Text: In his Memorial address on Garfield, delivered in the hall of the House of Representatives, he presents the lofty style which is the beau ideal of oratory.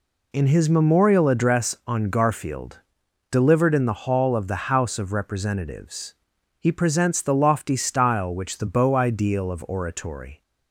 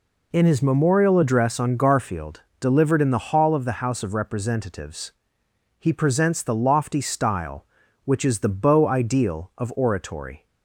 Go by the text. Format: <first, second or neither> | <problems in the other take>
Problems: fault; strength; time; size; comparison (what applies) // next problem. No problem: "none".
second | skips "is"; at 8.5 s